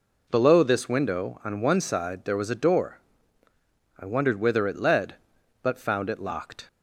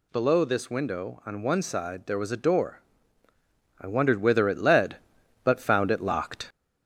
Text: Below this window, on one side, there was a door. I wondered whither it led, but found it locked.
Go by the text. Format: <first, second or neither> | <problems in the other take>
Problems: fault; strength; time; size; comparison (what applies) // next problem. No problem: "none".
first | gets louder; slight; throughout; 2.5 dB